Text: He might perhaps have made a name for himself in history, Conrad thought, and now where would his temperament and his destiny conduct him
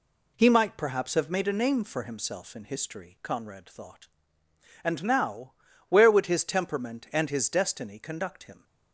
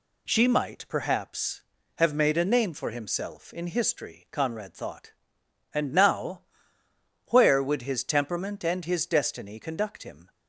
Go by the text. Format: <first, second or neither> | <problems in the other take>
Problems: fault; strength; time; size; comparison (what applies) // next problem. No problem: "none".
first | says "She" for "He"; at 0.2 s // pauses between "now" and "where"; noticeable; at 6.4 s; 0.86 s long; slight in the first